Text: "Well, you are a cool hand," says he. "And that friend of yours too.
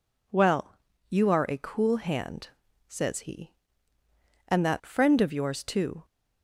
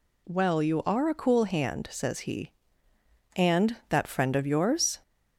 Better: first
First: none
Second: stops before "too"; at 5.0 s

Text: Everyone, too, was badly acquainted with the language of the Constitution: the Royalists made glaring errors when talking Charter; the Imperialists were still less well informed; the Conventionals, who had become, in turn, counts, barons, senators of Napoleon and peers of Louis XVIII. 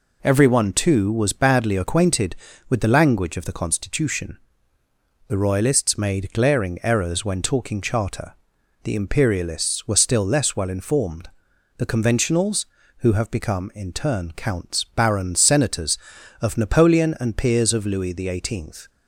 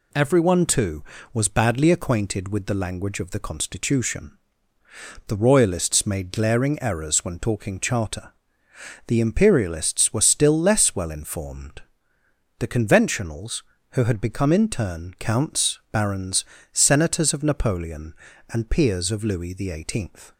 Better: second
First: says "have" for "had"; at 13.1 s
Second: none

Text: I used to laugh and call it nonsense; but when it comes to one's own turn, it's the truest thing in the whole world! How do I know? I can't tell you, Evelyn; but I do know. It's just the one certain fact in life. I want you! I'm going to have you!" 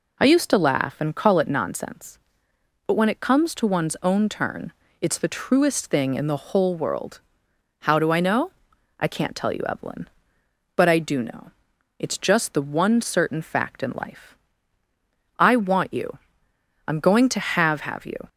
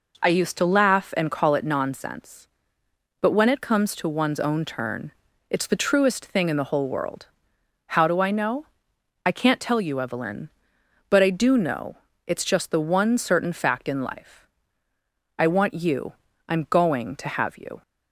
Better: second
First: says "have" twice; at 17.8 s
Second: none

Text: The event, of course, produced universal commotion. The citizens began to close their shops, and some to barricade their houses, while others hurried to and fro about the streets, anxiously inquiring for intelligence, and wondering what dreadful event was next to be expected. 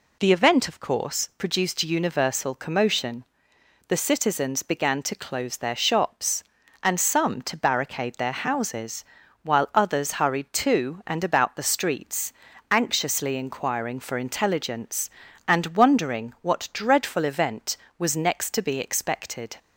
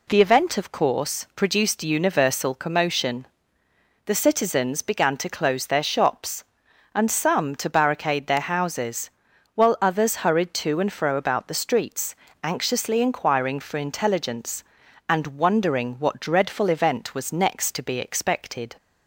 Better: second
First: skips "fro"; at 11.2 s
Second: none

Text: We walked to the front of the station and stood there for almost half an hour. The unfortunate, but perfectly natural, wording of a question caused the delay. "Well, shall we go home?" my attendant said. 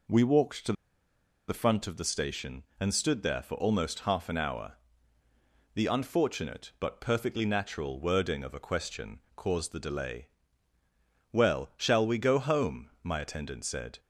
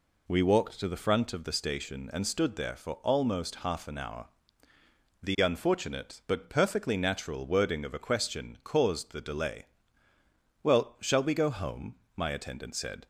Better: second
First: pauses between "to" and "the"; noticeable; at 0.7 s; 0.75 s long // pauses between "question" and "caused"; slight; at 9.1 s; 0.16 s long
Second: none

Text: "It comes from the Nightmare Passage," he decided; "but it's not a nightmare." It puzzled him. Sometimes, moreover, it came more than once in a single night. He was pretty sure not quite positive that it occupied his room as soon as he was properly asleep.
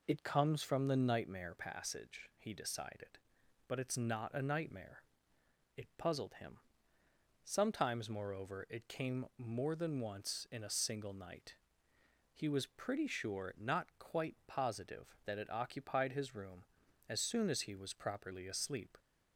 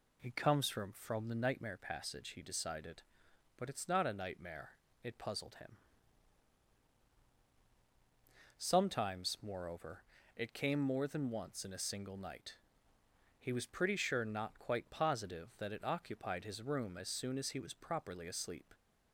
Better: first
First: none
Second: says "from" twice; at 0.9 s

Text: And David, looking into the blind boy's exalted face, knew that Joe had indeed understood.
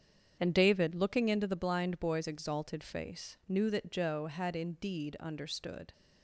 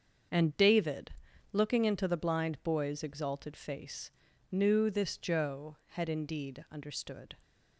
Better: first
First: starts louder than the rest; strong; until 1.4 s; 8 dB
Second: starts louder than the rest; until 1.7 s; 7 dB // says "this" for "that"; at 4.8 s

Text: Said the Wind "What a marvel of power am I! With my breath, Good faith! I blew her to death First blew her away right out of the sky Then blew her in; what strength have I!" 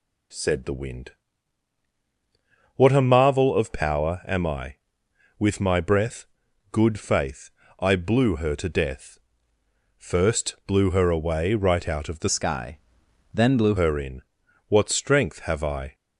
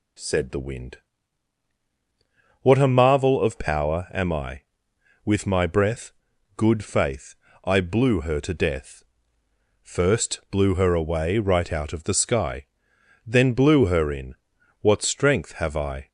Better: second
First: pauses between "Wind" and "What"; strong; at 1.1 s; 1.6 s long // pauses between "death" and "First"; noticeable; at 9.1 s; 0.78 s long // changes voice from "sky" to "blew"; from 12.2 to 13.7 s; 1.5 s long // pauses between "sky" and "Then"; noticeable; at 12.7 s; 0.56 s long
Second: pauses between "Wind" and "What"; strong; at 0.9 s; 1.6 s long // pauses between "death" and "First"; noticeable; at 9.0 s; 0.78 s long // pauses between "sky" and "Then"; noticeable; at 12.6 s; 0.62 s long

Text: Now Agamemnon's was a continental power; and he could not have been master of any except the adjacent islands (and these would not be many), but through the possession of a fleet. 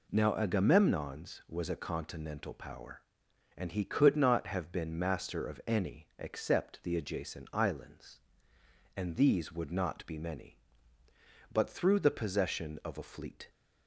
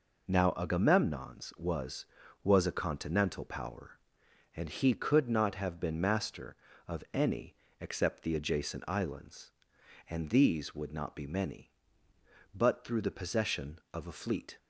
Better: first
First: none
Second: says "was" twice; at 2.4 s // pauses between "any" and "except"; slight; at 7.5 s; 0.24 s long

